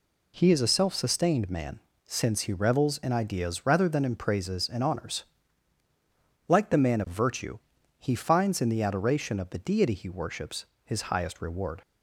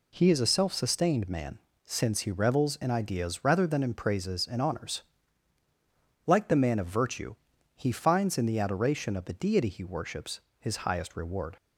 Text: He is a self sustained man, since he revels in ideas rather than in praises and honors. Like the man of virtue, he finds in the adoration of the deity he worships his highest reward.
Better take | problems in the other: neither | pauses between "worships" and "his"; slight; the same in both

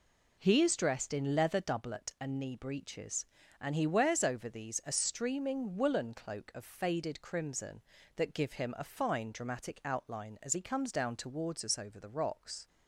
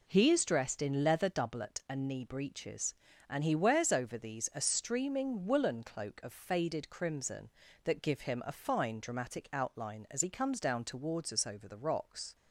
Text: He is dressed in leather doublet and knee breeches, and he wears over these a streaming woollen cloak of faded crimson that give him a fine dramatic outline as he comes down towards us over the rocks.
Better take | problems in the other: neither | none

